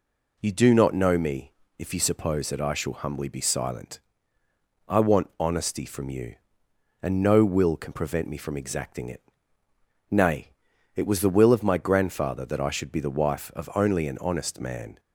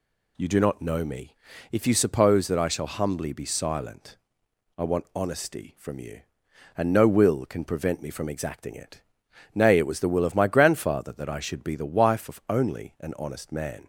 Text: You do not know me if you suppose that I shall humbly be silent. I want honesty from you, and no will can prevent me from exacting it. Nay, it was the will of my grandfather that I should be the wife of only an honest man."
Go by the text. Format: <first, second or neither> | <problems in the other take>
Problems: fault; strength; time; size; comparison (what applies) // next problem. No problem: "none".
neither | pauses between "me" and "if"; slight; the same in both